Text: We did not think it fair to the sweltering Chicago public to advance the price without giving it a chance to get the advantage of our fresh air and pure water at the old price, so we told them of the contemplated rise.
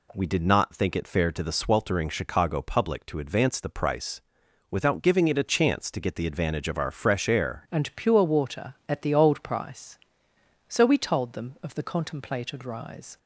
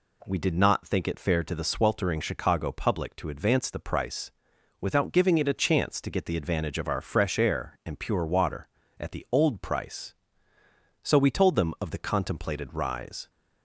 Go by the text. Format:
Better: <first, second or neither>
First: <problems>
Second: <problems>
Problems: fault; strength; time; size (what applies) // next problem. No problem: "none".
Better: second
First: pauses between "price" and "without"; noticeable; at 4.2 s; 0.50 s long // changes voice at "and"; from 7.6 s on; 5.5 s long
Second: pauses between "price" and "without"; noticeable; at 4.3 s; 0.50 s long